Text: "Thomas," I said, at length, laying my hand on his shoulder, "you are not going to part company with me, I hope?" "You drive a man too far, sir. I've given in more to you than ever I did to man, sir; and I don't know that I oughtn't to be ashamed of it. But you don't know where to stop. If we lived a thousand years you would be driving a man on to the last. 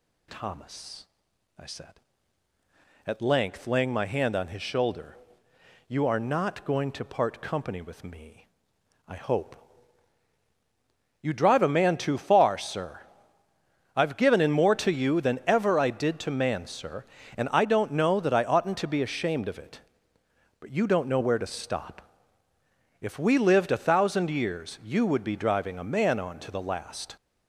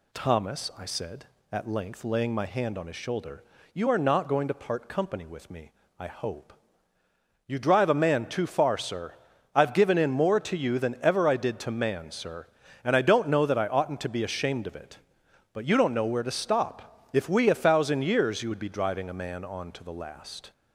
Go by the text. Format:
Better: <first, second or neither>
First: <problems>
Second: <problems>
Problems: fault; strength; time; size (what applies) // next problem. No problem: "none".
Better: first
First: none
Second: skips "lived"; at 17.4 s